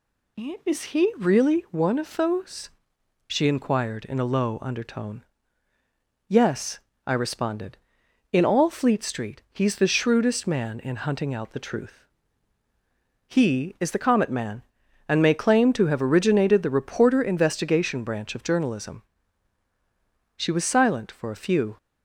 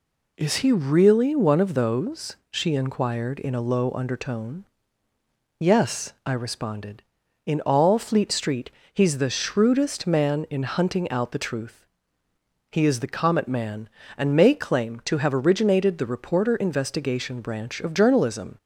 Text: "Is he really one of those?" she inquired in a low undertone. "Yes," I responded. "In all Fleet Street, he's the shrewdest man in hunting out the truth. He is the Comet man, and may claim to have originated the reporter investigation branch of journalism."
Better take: second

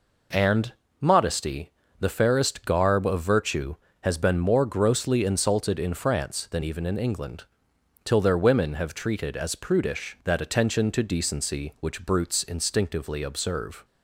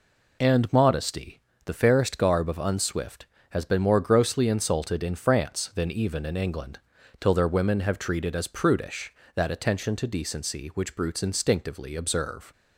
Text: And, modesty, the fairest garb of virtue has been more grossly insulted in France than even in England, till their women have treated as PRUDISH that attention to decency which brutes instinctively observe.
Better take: first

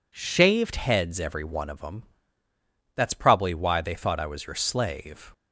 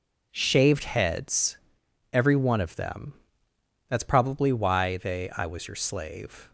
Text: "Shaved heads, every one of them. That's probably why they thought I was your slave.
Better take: first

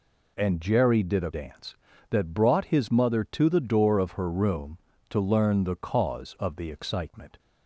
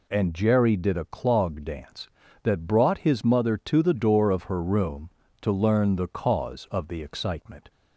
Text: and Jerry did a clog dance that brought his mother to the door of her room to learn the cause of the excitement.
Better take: second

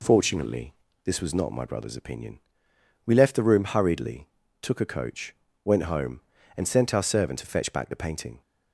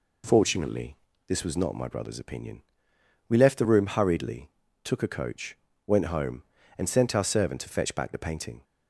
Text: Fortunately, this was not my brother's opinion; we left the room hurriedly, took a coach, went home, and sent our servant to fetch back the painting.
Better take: neither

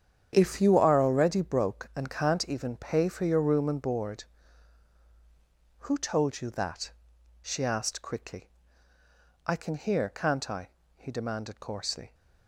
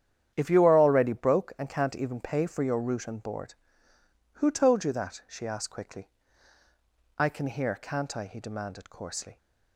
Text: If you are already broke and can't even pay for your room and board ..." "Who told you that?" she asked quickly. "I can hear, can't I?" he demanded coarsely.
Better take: first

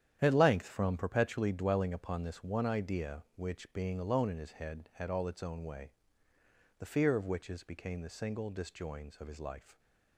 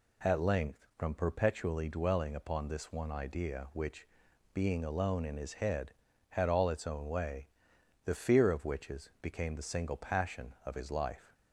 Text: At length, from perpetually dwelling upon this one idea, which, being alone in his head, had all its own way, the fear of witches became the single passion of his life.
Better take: second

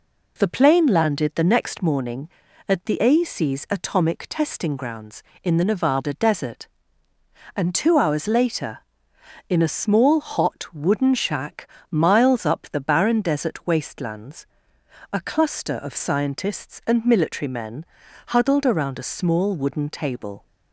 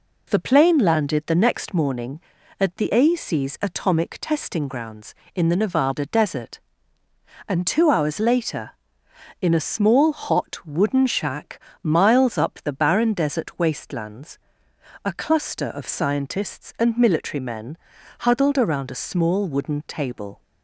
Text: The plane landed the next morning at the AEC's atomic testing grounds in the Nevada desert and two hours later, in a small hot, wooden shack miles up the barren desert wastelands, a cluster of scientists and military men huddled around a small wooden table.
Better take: neither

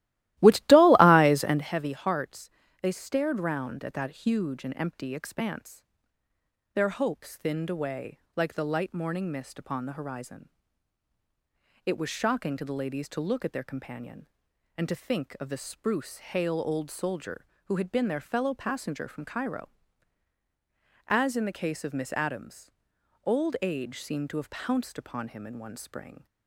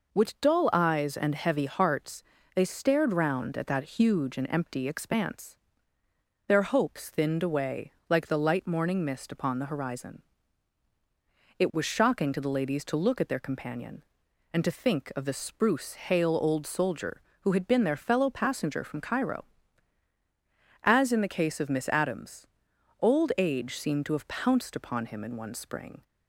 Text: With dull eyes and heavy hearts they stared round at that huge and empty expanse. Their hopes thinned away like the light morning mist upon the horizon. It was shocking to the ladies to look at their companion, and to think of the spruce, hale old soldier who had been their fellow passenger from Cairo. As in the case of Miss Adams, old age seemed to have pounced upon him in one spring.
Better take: second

